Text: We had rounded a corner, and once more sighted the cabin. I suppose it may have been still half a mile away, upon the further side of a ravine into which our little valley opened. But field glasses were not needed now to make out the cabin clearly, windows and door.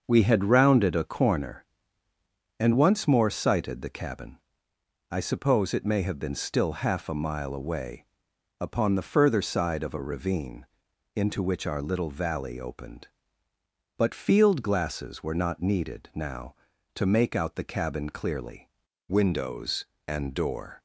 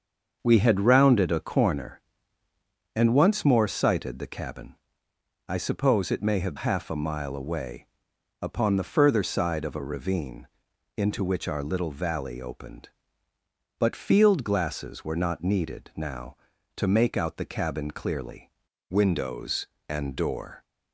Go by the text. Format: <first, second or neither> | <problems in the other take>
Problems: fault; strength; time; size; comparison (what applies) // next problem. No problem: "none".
first | starts louder than the rest; until 1.4 s; 6.5 dB; also in the first // skips "been still"; at 6.5 s // pauses between "ravine" and "into"; noticeable; at 10.4 s; 0.48 s long; noticeable in the first